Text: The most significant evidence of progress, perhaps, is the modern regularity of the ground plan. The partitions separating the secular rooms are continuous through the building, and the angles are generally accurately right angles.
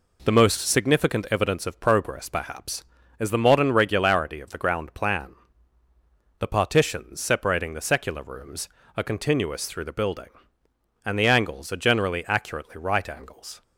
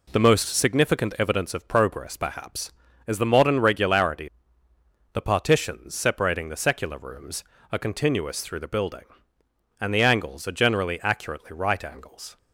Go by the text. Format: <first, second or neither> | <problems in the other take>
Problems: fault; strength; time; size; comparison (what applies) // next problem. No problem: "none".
first | skips "of the ground plan"; at 4.7 s